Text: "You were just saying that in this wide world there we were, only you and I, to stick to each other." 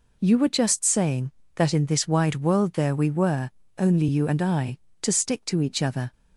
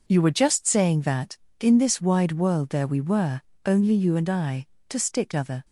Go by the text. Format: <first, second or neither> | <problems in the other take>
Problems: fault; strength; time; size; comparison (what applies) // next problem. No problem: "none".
first | skips "to each"; at 5.3 s